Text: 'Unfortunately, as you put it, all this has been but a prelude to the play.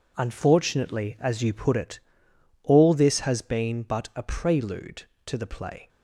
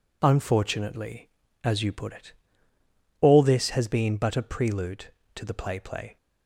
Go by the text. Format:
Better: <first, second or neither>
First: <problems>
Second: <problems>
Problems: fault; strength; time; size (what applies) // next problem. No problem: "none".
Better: first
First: none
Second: says "play" twice; at 5.7 s